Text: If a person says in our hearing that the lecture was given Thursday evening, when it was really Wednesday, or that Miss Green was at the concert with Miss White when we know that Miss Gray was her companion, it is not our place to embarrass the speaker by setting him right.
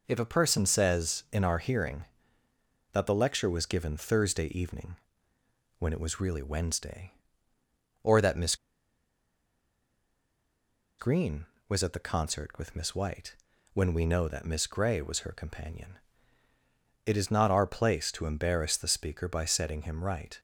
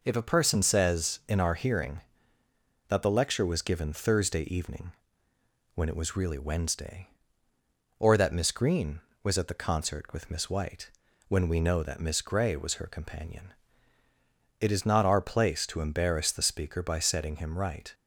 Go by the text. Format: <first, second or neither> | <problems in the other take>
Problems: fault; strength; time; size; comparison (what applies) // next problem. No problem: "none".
second | pauses between "Miss" and "Green"; strong; at 8.5 s; 2.4 s long // pauses between "White" and "when"; at 13.3 s; 0.38 s long; also in the second